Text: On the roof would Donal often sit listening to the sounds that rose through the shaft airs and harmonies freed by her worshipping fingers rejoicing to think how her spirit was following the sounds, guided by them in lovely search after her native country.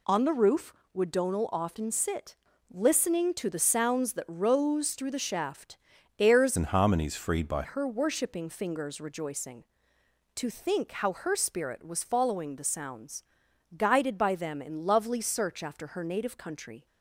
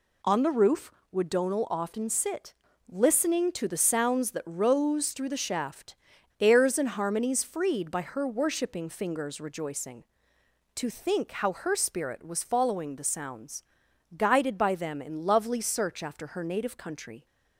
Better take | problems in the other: second | pauses between "sit" and "listening"; slight; at 2.3 s; 0.36 s long; slight in the second // pauses between "shaft" and "airs"; at 5.7 s; 0.44 s long; noticeable in the second // changes voice from "and" to "by"; from 6.5 to 7.6 s; 1.1 s long

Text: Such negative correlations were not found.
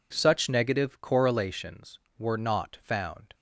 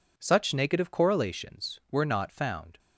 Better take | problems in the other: neither | none

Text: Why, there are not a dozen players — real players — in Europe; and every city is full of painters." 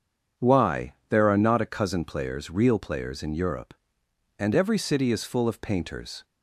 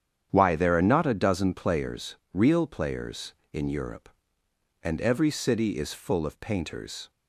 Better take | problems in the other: second | starts louder than the rest; strong; until 1.5 s; 7.5 dB; strong in the second // says "cousin" for "dozen"; at 1.6 s

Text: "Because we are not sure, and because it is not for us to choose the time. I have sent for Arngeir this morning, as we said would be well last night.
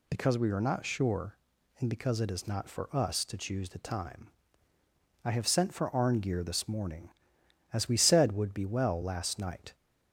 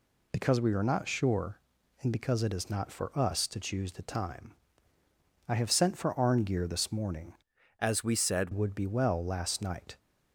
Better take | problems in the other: first | changes voice from "as" to "said"; from 7.7 to 8.5 s; 0.8 s long

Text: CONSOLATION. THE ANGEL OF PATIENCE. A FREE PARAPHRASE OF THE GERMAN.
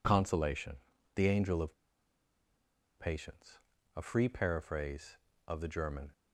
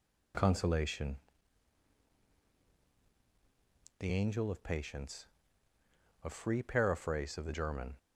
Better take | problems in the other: second | pauses between "OF" and "PATIENCE"; at 1.7 s; 1.2 s long

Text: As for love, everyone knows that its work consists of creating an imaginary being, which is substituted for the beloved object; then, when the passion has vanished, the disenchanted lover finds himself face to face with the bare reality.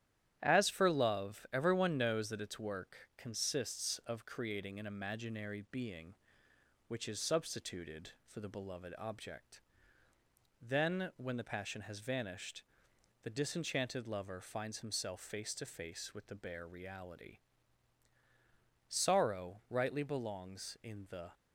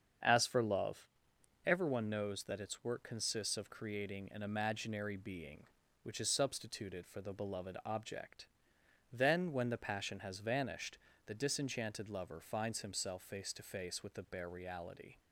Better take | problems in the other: second | starts louder than the rest; strong; until 1.4 s; 11 dB; strong in the second // goes on to say "Sorrow rightly belongs in the"; strong; from 18.8 s on; 2.4 s long

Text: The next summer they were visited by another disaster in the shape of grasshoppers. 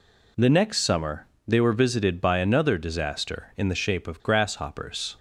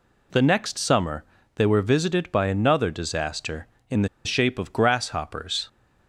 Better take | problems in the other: first | pauses between "summer" and "they"; slight; at 1.2 s; 0.30 s long; slight in the first // pauses between "the" and "shape"; slight; at 4.0 s; 0.17 s long

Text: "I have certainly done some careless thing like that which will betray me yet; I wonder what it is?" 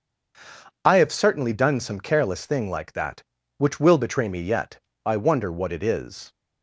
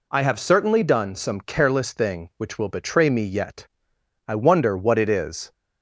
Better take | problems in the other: first | skips "like that"; at 2.3 s

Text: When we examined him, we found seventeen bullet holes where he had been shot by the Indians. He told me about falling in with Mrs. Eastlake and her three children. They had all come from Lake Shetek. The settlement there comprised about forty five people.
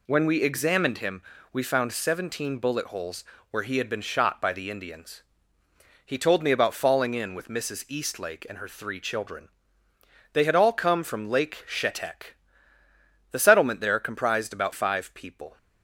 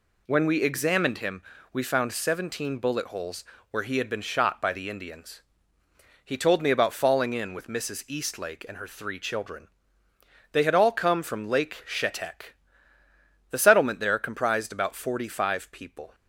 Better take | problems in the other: second | pauses between "holes" and "where"; slight; at 3.2 s; 0.26 s long; slight in the second // skips "forty"; at 14.7 s

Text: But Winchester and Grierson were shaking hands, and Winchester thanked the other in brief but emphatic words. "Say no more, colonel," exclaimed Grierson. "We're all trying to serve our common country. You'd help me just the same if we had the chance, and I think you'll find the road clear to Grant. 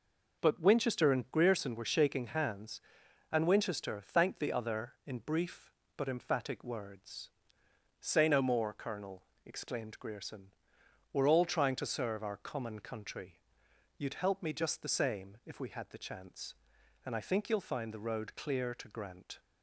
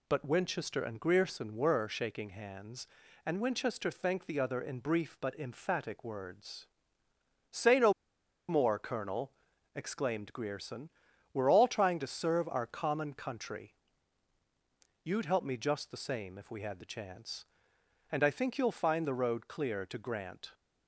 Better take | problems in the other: first | pauses between "no" and "more"; noticeable; at 7.9 s; 0.56 s long

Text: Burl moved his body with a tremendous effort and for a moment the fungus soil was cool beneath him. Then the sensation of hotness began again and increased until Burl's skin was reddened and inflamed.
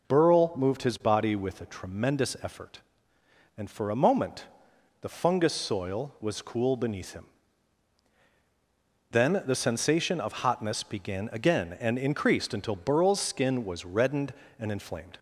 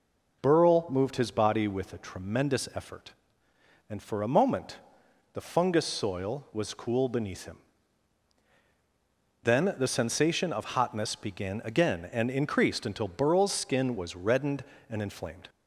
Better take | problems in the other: neither | pauses between "moment" and "the"; noticeable; the same in both

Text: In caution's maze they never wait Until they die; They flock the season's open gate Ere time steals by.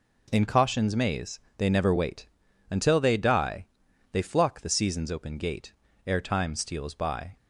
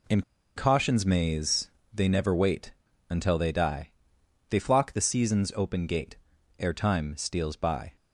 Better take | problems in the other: first | pauses between "In" and "caution's"; slight; at 0.2 s; 0.35 s long // pauses between "maze" and "they"; slight; at 1.6 s; 0.22 s long; slight in the first // pauses between "wait" and "Until"; at 2.7 s; 0.38 s long; also in the first // pauses between "gate" and "Ere"; at 6.1 s; 0.42 s long; slight in the first

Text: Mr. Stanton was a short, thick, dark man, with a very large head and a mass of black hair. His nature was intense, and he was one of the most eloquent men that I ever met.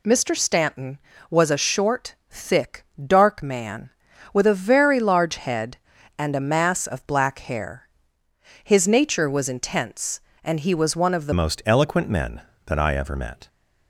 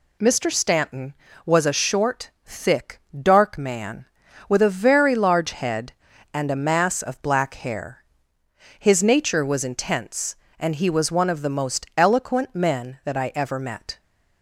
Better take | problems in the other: second | changes voice at "most"; from 11.3 s on; 2.1 s long

